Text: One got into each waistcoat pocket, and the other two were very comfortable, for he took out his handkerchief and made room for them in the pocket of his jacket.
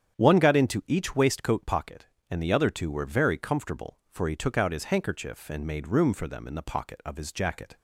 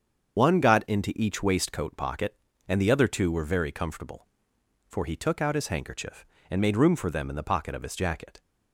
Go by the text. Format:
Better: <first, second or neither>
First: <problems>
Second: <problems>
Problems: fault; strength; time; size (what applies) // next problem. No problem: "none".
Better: first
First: starts louder than the rest; strong; until 1.1 s; 8.5 dB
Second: loses the start of "One"; at 0.3 s; 125 ms // starts louder than the rest; strong; until 1.4 s; 7.5 dB